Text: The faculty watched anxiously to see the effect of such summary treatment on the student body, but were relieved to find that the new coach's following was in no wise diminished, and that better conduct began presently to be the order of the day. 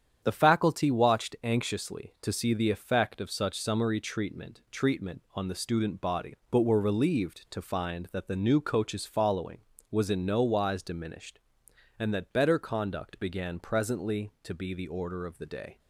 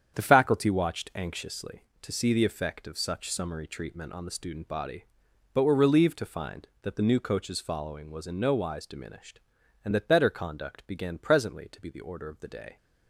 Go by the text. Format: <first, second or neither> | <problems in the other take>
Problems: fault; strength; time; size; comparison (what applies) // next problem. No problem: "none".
second | starts louder than the rest; strong; until 1.2 s; 8.5 dB; strong in the second // says "treatment" twice; at 4.7 s